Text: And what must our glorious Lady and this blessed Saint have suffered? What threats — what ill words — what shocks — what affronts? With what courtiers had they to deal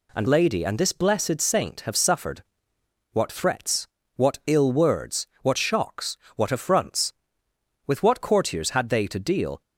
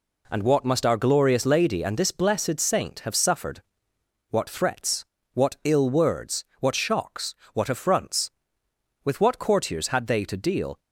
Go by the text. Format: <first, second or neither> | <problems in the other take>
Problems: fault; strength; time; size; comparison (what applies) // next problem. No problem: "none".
second | skips "what must our glorious"; at 0.2 s